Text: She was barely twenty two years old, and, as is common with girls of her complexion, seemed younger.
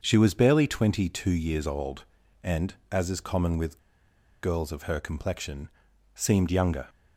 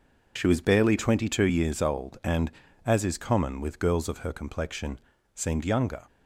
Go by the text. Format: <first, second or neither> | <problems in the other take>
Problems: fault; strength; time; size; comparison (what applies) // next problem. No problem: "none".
second | starts louder than the rest; until 1.0 s; 6.5 dB // pauses between "with" and "girls"; noticeable; at 3.7 s; 0.65 s long